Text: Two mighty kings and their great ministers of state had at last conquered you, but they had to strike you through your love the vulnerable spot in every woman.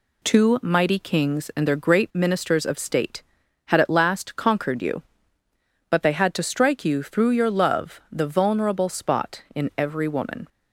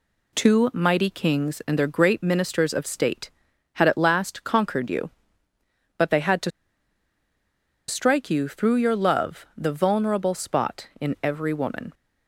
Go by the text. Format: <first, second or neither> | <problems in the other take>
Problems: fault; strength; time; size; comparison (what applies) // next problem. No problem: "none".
first | pauses between "to" and "strike"; strong; at 6.4 s; 1.3 s long